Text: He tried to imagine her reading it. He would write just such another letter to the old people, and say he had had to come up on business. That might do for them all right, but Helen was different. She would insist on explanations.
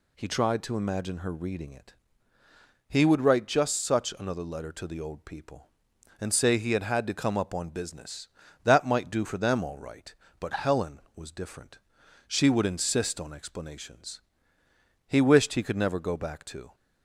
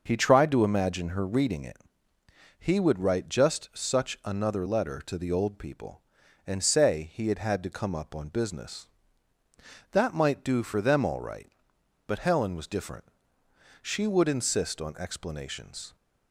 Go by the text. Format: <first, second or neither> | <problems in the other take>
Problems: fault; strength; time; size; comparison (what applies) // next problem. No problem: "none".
second | goes on to say "He wished he could never go back to"; from 15.0 s on; 1.6 s long